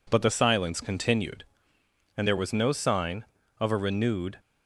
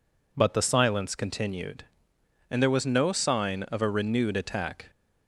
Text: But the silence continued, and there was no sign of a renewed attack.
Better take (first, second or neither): second